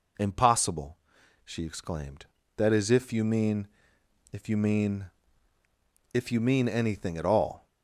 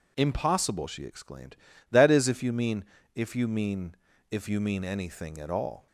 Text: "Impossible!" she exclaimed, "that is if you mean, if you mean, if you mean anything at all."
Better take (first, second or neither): neither